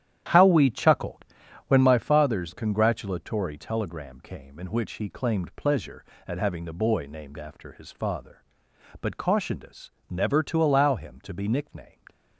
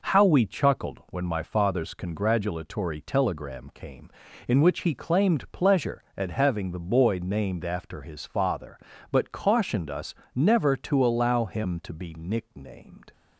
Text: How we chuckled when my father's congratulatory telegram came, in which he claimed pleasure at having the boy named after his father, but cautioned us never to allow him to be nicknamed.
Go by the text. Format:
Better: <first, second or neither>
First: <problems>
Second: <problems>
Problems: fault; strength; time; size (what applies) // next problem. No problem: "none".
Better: second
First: starts louder than the rest; strong; until 1.9 s; 11 dB // pauses between "chuckled" and "when"; noticeable; at 1.2 s; 0.46 s long // pauses between "us" and "never"; slight; at 9.8 s; 0.20 s long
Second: pauses between "us" and "never"; slight; at 10.1 s; 0.22 s long